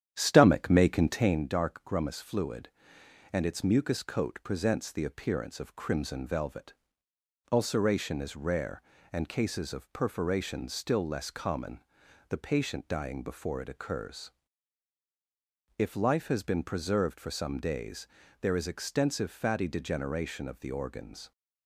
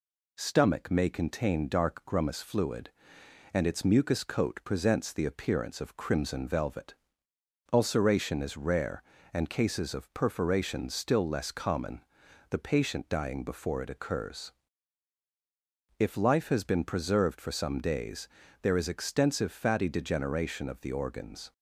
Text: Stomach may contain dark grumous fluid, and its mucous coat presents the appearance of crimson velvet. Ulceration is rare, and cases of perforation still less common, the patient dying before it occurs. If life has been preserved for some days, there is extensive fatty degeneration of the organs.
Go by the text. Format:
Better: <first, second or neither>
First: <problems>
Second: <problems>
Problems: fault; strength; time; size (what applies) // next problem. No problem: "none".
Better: second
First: starts louder than the rest; strong; until 1.5 s; 10 dB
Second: none